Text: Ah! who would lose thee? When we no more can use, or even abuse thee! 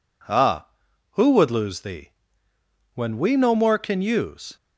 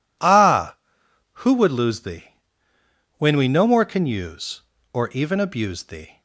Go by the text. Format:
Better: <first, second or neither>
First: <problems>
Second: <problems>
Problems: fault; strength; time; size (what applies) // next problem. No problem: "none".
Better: second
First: stops before "or even abuse thee"; at 4.5 s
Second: none